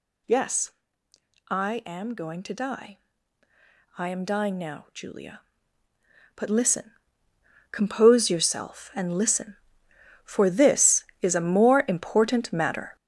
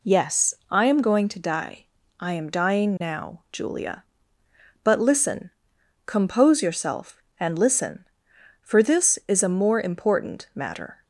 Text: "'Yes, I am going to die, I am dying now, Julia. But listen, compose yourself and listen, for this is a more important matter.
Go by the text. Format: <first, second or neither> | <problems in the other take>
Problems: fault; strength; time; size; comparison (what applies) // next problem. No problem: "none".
second | gets louder; throughout; 6 dB